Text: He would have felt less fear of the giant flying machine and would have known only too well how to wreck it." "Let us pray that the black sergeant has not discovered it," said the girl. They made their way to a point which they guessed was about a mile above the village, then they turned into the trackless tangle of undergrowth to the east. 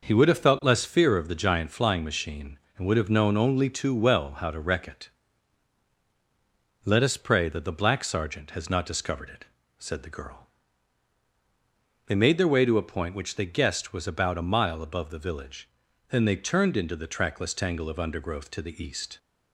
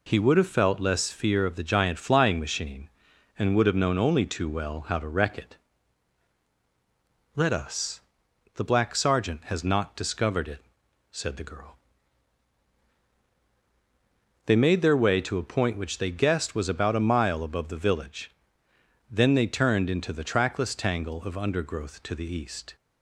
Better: first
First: none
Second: skips "pray that"; at 8.2 s

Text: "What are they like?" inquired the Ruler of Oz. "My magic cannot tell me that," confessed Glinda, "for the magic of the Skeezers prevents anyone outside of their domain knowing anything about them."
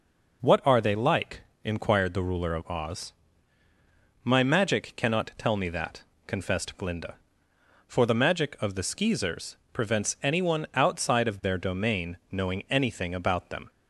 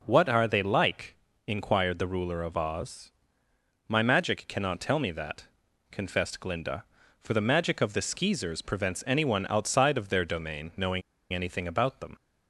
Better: first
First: none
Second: pauses between "knowing" and "anything"; slight; at 11.0 s; 0.31 s long

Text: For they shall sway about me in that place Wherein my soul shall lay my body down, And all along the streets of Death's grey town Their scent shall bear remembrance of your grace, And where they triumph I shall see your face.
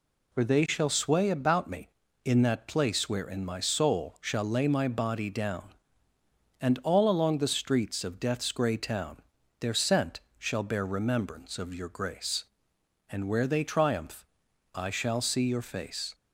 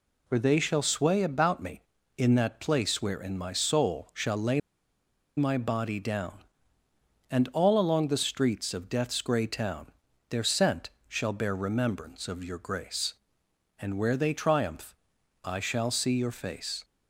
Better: first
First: pauses between "town" and "Their"; at 9.1 s; 0.44 s long // pauses between "scent" and "shall"; slight; at 10.2 s; 0.18 s long // pauses between "triumph" and "I"; noticeable; at 14.2 s; 0.52 s long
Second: pauses between "lay" and "my"; noticeable; at 4.5 s; 0.77 s long // pauses between "town" and "Their"; at 9.8 s; 0.44 s long // pauses between "scent" and "shall"; slight; at 10.9 s; 0.18 s long // pauses between "triumph" and "I"; noticeable; at 14.9 s; 0.52 s long

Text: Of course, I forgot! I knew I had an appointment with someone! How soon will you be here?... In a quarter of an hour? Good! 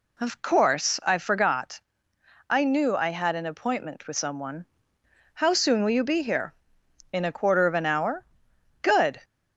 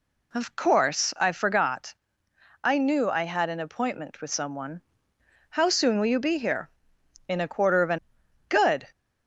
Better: first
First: none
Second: skips "hour"; at 8.2 s

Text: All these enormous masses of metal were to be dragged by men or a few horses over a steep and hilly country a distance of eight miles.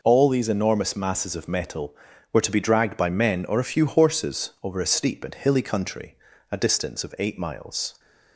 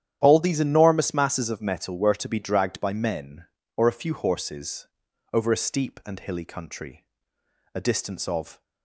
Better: first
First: pauses between "country" and "a"; slight; at 6.1 s; 0.36 s long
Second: starts louder than the rest; strong; until 1.2 s; 10.5 dB // pauses between "horses" and "over"; noticeable; at 4.8 s; 0.46 s long // pauses between "country" and "a"; noticeable; at 7.0 s; 0.70 s long // stops before "eight miles"; at 8.6 s

